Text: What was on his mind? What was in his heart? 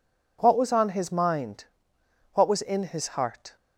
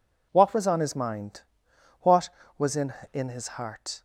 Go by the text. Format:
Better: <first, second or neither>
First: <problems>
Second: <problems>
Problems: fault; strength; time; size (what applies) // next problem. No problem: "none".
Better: first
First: none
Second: says "in" twice; at 3.1 s